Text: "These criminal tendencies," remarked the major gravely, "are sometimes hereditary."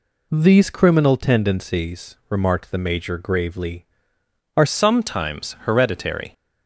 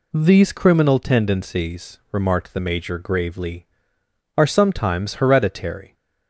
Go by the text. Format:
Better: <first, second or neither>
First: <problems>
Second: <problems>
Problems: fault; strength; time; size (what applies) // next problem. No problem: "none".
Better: second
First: changes voice at "sometimes"; from 4.6 s on; 1.7 s long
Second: none